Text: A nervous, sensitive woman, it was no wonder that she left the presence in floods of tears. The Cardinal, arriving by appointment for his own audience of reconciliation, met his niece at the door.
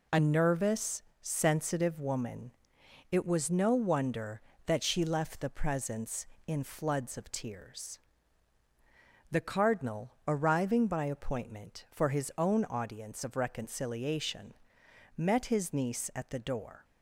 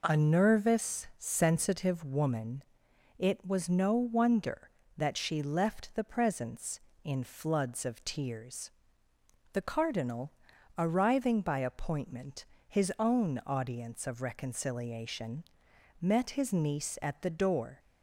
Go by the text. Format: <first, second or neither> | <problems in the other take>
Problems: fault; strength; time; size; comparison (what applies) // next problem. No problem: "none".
first | skips "for"; at 12.5 s